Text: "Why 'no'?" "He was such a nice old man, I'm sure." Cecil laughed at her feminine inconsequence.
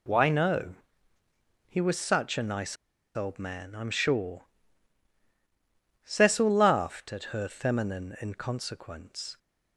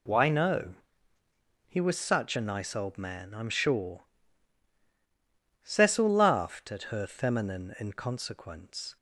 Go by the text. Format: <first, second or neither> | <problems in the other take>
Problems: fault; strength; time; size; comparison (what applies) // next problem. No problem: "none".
second | pauses between "nice" and "old"; at 2.7 s; 0.40 s long